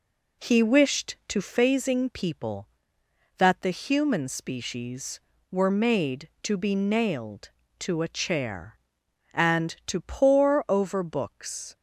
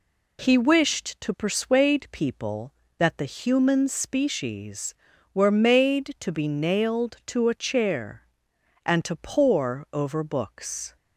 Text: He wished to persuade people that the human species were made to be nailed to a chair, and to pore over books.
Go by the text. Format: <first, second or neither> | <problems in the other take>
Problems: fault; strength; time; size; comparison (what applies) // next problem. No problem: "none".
second | says "phasing" for "persuade"; at 1.4 s